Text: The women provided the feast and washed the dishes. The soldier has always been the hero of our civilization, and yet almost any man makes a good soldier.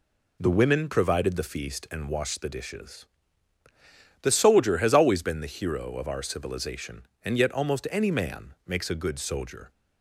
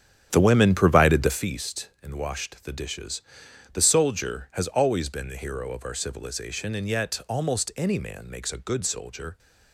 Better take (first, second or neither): first